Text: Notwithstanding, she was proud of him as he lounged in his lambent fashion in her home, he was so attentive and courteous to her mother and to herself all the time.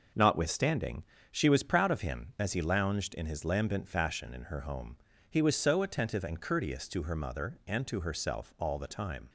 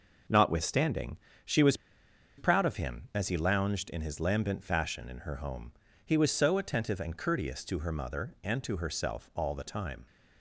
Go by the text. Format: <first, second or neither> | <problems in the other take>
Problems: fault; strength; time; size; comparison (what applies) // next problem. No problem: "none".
first | pauses between "was" and "proud"; noticeable; at 1.7 s; 0.60 s long